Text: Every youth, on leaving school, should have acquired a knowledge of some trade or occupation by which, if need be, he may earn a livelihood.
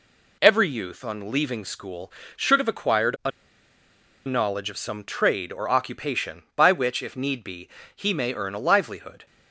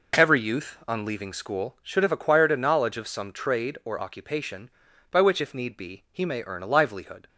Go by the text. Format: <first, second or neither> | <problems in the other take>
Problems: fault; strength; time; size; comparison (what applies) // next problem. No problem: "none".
second | pauses between "a" and "knowledge"; noticeable; at 3.3 s; 0.95 s long